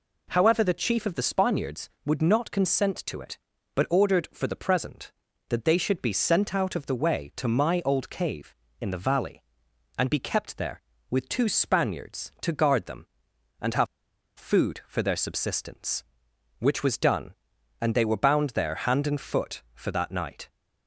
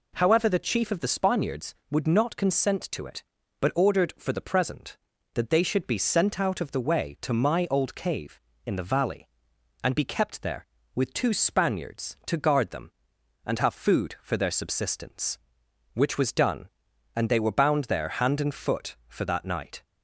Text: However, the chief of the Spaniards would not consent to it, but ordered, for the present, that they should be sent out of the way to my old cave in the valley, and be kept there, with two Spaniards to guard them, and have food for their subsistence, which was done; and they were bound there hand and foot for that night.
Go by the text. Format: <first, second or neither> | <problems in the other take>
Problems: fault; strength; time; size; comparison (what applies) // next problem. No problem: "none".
second | pauses between "have" and "food"; noticeable; at 13.8 s; 0.52 s long